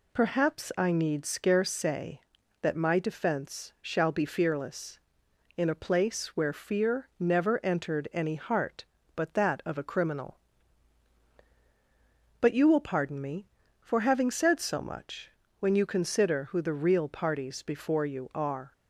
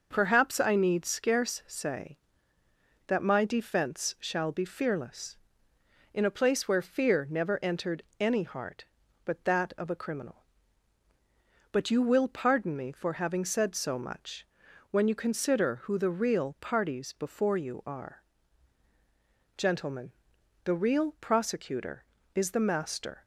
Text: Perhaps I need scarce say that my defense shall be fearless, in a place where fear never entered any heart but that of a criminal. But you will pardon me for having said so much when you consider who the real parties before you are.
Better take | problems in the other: first | pauses between "entered" and "any"; slight; at 8.0 s; 0.16 s long // pauses between "much" and "when"; at 14.4 s; 0.44 s long; slight in the first // goes on to say "Gentlemen the real prosecutor is the master"; strong; from 19.5 s on; 3.6 s long

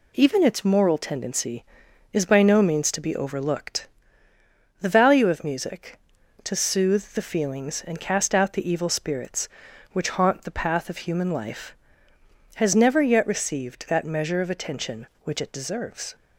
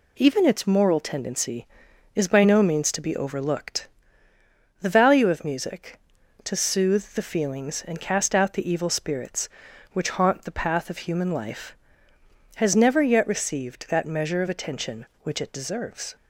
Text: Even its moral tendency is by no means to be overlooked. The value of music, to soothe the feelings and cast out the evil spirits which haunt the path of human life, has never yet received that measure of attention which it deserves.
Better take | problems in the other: neither | none

